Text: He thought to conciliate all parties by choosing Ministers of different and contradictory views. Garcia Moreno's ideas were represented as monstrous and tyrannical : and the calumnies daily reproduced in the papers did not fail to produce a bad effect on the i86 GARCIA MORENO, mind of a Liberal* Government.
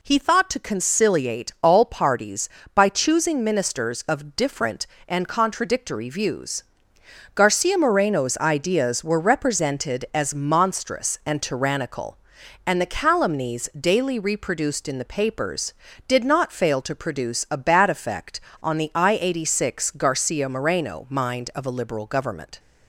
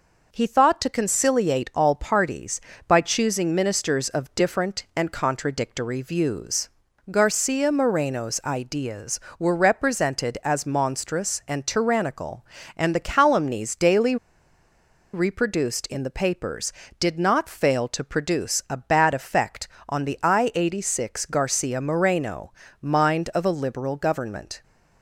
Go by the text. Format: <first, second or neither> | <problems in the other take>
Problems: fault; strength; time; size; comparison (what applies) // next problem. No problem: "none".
first | pauses between "daily" and "reproduced"; noticeable; at 14.1 s; 0.97 s long